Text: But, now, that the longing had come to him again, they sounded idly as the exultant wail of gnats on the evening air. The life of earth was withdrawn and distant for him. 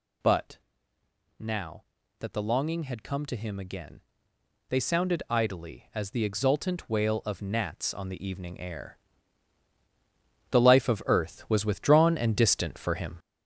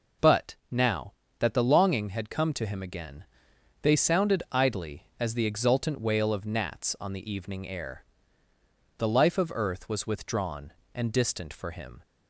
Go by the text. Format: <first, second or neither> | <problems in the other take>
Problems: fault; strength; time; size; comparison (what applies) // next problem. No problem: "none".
second | gets louder; throughout; 6.5 dB